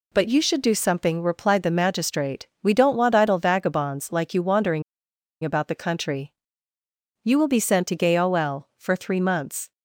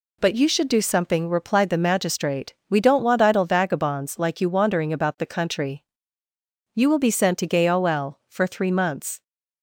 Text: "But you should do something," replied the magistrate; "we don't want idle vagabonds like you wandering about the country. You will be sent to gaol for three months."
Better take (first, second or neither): second